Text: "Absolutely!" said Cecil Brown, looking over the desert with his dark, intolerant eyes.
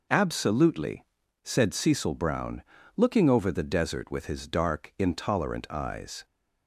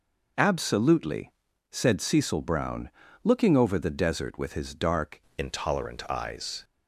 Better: first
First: none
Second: changes voice at "intolerant"; from 5.3 s on; 1.3 s long

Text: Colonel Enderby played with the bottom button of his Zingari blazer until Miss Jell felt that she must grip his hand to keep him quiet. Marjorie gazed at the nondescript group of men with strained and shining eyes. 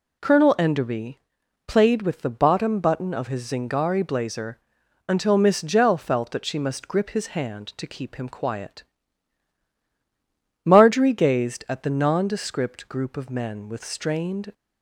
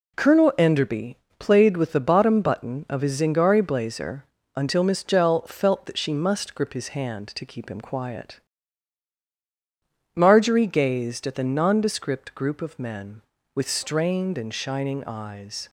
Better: second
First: pauses between "Enderby" and "played"; noticeable; at 1.1 s; 0.48 s long // pauses between "blazer" and "until"; noticeable; at 4.5 s; 0.50 s long // stops before "and shining eyes"; at 14.5 s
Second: pauses between "Enderby" and "played"; slight; at 1.1 s; 0.22 s long // pauses between "blazer" and "until"; slight; at 4.2 s; 0.30 s long

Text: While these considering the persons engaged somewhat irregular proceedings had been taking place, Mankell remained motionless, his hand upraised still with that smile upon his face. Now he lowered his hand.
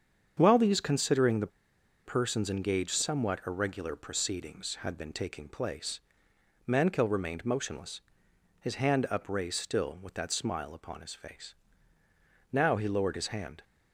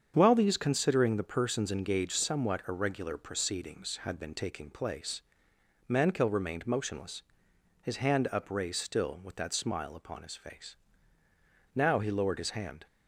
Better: second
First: starts louder than the rest; strong; until 1.3 s; 7.5 dB // pauses between "the" and "persons"; noticeable; at 1.4 s; 0.57 s long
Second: starts louder than the rest; strong; until 1.1 s; 7.5 dB

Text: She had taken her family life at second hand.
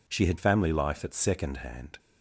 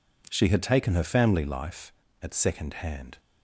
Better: second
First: skips "taken her"; at 0.3 s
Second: none

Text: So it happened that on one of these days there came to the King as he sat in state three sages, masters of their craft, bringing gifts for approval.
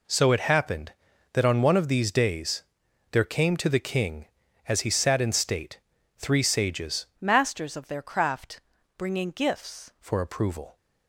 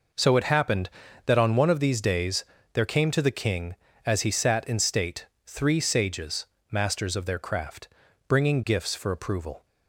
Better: second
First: pauses between "days" and "there"; noticeable; at 2.6 s; 0.50 s long // pauses between "state" and "three"; at 5.7 s; 0.38 s long // changes voice from "masters" to "gifts"; from 7.2 to 9.9 s; 2.7 s long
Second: pauses between "days" and "there"; slight; at 2.4 s; 0.28 s long // pauses between "state" and "three"; slight; at 5.2 s; 0.18 s long

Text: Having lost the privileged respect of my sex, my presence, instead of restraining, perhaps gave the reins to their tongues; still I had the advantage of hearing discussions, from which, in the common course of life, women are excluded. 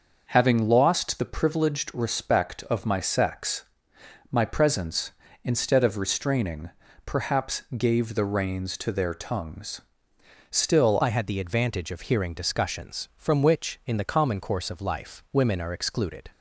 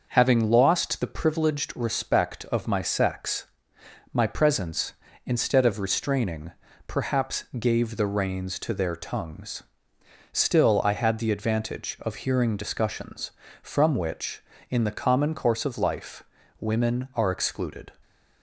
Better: second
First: starts louder than the rest; noticeable; until 1.3 s; 6 dB // pauses between "perhaps" and "gave"; slight; at 7.6 s; 0.16 s long // changes voice at "I"; from 11.0 s on; 5.3 s long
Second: starts louder than the rest; noticeable; until 1.1 s; 6 dB // pauses between "perhaps" and "gave"; slight; at 7.4 s; 0.16 s long

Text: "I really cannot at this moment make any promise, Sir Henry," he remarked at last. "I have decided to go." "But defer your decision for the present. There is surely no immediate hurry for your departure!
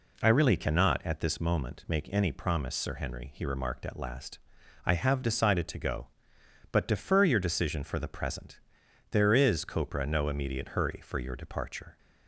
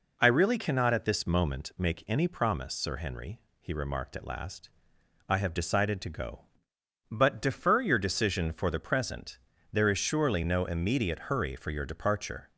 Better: second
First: says "copra" for "surely"; at 9.6 s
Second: none

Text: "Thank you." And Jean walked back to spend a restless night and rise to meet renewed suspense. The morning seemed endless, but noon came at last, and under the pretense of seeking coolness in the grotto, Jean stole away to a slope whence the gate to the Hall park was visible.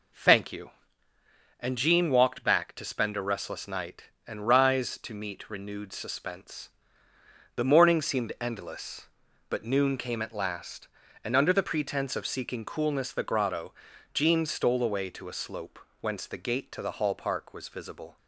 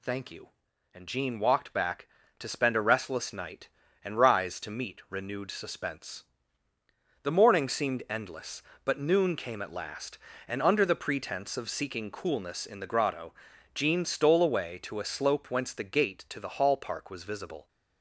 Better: second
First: skips "in"; at 13.1 s // pauses between "slope" and "whence"; slight; at 15.7 s; 0.22 s long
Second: none

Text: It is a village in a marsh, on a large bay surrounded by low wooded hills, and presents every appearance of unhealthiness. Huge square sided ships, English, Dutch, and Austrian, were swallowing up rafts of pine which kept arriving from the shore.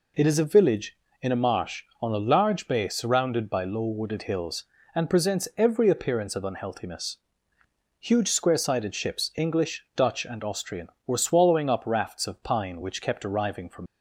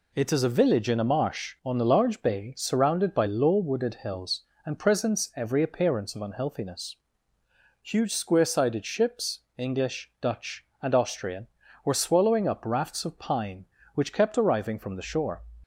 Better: second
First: stops before "the shore"; at 13.8 s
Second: none

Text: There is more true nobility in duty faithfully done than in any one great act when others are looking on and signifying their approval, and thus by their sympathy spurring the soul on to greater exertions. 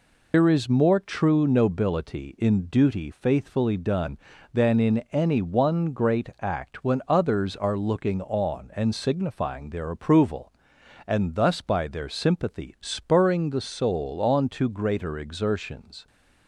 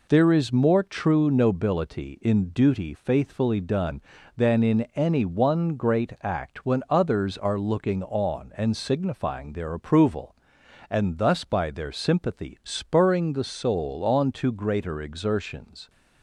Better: second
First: loses the start of "There"; at 0.3 s; 80 ms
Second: none

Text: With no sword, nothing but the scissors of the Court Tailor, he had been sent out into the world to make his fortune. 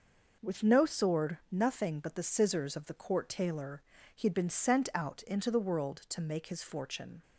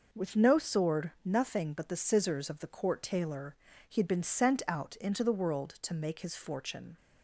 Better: neither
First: none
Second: none

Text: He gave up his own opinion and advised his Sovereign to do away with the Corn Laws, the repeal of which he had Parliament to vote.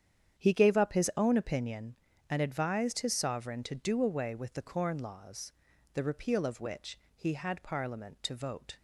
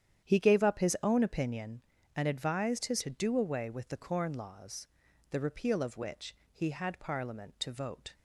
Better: first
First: starts louder than the rest; strong; until 1.4 s; 9 dB // pauses between "which" and "he"; slight; at 6.9 s; 0.16 s long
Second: starts louder than the rest; strong; until 1.3 s; 9.5 dB // skips "Sovereign"; at 3.0 s // pauses between "which" and "he"; slight; at 6.3 s; 0.16 s long

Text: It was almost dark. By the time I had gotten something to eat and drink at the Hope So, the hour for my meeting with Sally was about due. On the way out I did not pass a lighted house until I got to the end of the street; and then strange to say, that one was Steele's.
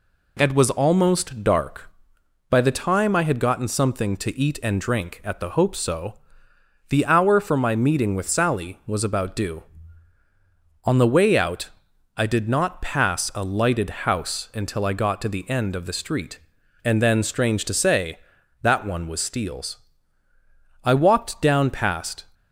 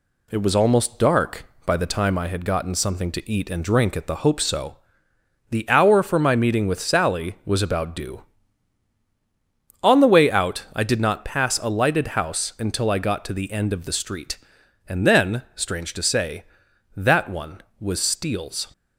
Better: second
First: pauses between "out" and "I"; noticeable; at 11.6 s; 0.46 s long // goes on to say "I walked down past"; from 20.8 s on; 1.4 s long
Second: none

